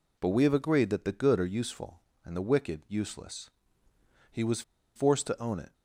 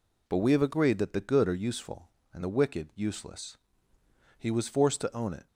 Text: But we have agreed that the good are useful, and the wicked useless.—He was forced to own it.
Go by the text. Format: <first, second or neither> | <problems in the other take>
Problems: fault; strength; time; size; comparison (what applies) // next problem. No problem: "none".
second | pauses between "was" and "forced"; slight; at 4.6 s; 0.34 s long